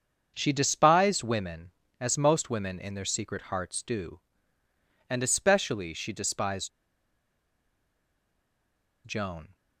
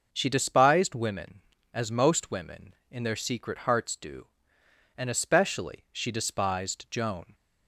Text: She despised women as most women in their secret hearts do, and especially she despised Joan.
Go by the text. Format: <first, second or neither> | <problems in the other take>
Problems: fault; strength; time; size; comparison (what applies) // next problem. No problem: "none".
second | starts louder than the rest; until 1.3 s; 7 dB // pauses between "despised" and "Joan"; strong; at 6.7 s; 2.3 s long